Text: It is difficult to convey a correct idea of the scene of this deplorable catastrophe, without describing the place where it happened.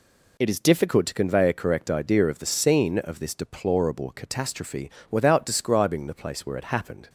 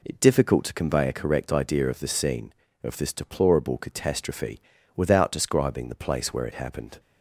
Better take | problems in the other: first | skips "is"; at 0.1 s

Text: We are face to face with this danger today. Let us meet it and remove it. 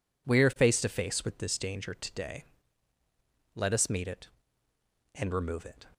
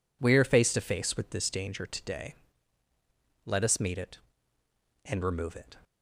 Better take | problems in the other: neither | none

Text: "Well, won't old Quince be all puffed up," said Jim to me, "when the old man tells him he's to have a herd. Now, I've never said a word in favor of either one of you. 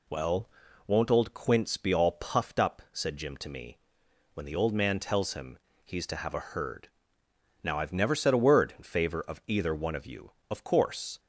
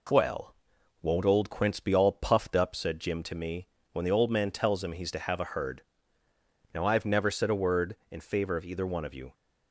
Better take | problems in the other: second | pauses between "him" and "he's"; slight; at 5.5 s; 0.26 s long // goes on to say "Of course"; noticeable; from 10.4 s on; 0.70 s long

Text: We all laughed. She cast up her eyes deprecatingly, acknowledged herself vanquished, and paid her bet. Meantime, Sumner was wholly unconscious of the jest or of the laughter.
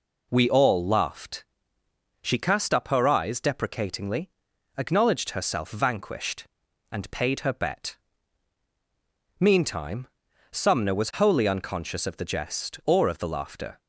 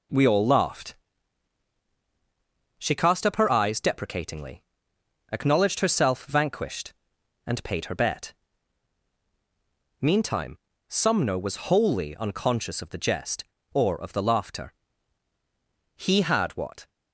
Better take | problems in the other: first | goes on to say "He had what"; noticeable; from 15.9 s on; 0.94 s long

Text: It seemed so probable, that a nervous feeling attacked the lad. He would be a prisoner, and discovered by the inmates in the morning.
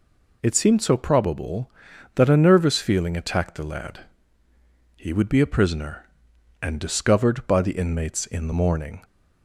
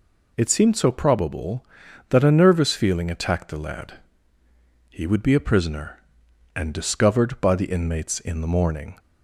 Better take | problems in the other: neither | none

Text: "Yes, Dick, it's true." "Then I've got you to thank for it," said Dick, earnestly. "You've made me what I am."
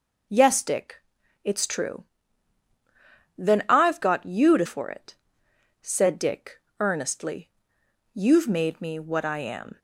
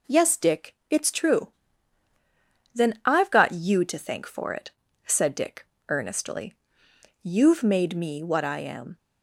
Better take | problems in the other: second | skips "thank"; at 4.6 s

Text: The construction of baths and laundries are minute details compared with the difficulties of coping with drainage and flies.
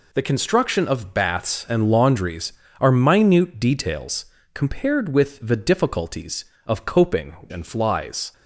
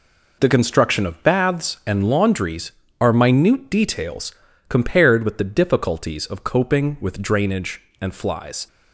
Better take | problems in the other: second | pauses between "details" and "compared"; slight; at 4.2 s; 0.28 s long; also in the second // skips "with drainage"; at 7.4 s

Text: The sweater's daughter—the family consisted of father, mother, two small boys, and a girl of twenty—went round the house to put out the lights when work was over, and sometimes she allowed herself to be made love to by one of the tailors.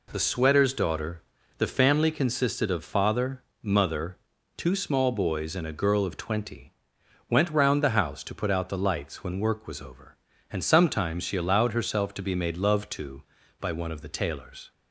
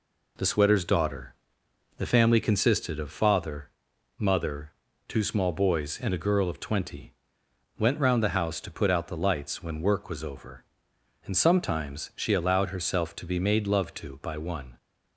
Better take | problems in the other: first | stops before "of the tailors"; at 14.7 s

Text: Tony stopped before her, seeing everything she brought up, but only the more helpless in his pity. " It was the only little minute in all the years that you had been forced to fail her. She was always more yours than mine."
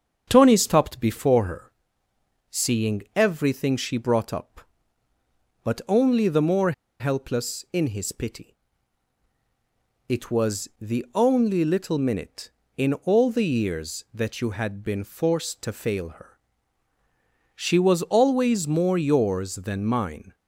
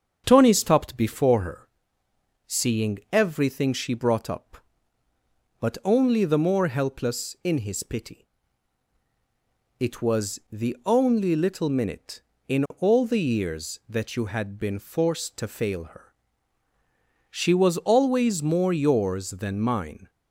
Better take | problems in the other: second | starts louder than the rest; strong; until 1.3 s; 7.5 dB; strong in the second // pauses between "more" and "helpless"; slight; at 6.7 s; 0.28 s long

